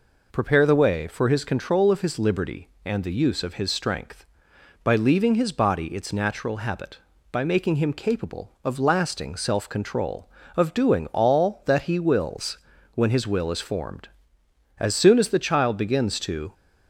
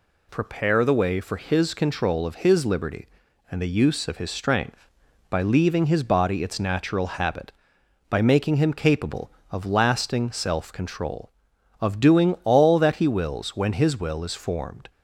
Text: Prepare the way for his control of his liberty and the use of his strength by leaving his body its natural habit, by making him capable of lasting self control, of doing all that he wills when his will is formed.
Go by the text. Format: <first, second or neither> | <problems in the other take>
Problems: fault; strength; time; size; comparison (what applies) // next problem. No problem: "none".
second | pauses between "wills" and "when"; at 12.5 s; 0.38 s long // goes on to say "As soon as the child begins to"; strong; from 14.7 s on; 1.7 s long